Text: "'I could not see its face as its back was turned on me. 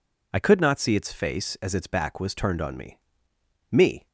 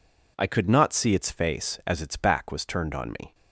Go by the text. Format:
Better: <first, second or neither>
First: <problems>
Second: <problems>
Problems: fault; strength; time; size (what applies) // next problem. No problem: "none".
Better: second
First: says "me" twice; at 3.6 s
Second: none